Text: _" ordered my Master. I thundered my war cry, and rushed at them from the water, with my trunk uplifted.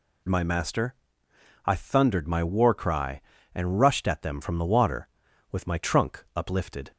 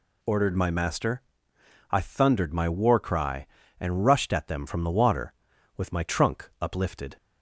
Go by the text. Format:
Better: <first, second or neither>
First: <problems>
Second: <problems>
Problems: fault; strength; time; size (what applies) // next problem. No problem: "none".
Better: second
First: skips "ordered"; at 0.2 s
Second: none